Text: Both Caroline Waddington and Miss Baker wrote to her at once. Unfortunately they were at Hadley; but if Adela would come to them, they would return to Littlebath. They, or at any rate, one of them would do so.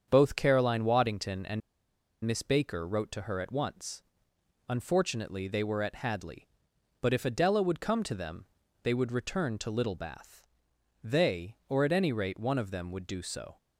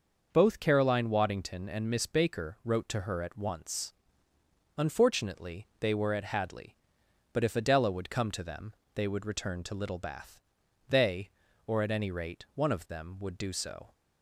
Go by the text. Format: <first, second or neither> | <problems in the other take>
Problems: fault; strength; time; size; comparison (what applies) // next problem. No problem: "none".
second | starts louder than the rest; strong; until 1.0 s; 7.5 dB; noticeable in the second // pauses between "and" and "Miss"; noticeable; at 1.6 s; 0.64 s long